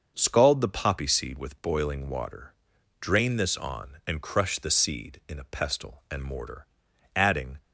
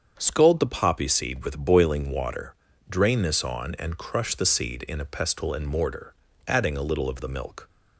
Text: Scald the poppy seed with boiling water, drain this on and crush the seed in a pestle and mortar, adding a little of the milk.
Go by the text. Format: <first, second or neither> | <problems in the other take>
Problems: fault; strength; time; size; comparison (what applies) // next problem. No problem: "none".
second | starts louder than the rest; until 1.1 s; 6.5 dB; strong in the second // stops before "a little of the milk"; at 7.5 s